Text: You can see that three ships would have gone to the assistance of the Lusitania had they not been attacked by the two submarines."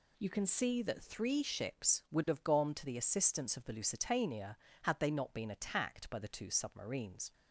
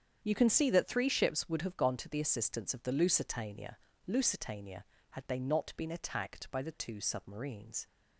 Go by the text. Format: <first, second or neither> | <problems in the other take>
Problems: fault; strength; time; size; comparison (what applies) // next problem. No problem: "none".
first | starts louder than the rest; strong; until 1.2 s; 8 dB // says "Lusitania" twice; at 4.0 s